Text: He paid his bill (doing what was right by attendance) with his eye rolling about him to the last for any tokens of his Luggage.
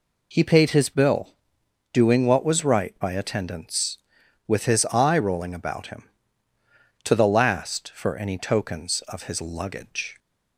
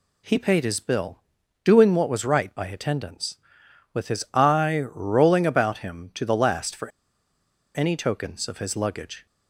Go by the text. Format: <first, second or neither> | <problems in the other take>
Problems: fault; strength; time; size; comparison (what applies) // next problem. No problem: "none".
first | pauses between "for" and "any"; noticeable; at 6.8 s; 0.88 s long